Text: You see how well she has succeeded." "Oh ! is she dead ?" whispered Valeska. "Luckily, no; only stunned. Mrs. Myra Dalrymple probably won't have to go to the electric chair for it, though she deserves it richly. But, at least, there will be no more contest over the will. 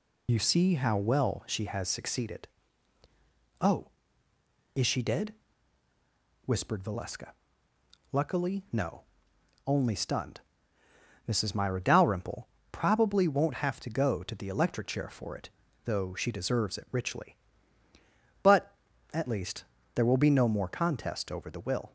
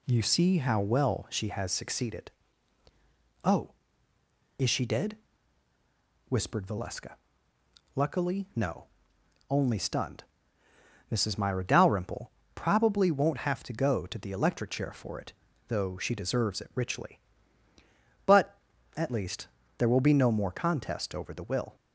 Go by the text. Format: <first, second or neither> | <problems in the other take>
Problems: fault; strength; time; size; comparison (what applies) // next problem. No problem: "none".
second | loses the start of "You"; at 0.2 s; 70 ms // pauses between "Dalrymple" and "probably"; slight; at 12.4 s; 0.20 s long; slight in the second